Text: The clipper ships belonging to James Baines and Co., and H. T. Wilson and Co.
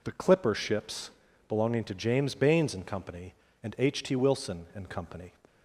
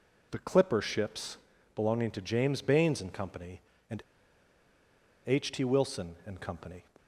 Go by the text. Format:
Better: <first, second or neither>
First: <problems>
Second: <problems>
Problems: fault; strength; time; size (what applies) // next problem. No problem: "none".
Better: first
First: pauses between "ships" and "belonging"; at 1.1 s; 0.38 s long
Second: pauses between "ships" and "belonging"; at 1.3 s; 0.38 s long // pauses between "and" and "H"; strong; at 4.0 s; 1.2 s long